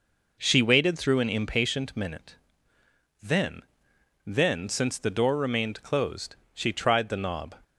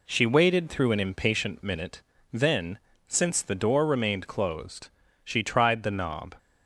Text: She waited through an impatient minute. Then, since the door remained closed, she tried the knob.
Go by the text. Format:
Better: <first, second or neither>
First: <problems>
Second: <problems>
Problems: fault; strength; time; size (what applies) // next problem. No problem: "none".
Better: second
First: says "Then" twice; at 4.2 s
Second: none